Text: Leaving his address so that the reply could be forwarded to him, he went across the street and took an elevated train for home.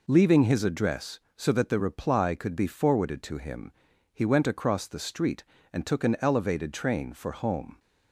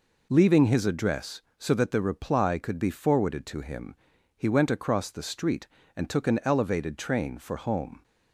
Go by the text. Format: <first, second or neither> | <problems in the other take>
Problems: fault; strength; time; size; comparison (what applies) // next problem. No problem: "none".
neither | none